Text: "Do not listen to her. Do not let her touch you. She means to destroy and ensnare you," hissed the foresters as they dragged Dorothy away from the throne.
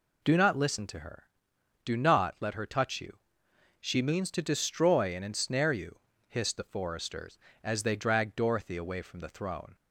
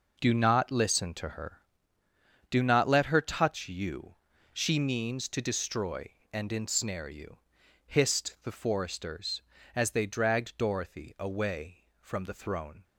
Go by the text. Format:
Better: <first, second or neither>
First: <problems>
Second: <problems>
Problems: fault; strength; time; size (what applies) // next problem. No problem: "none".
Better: neither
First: none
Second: none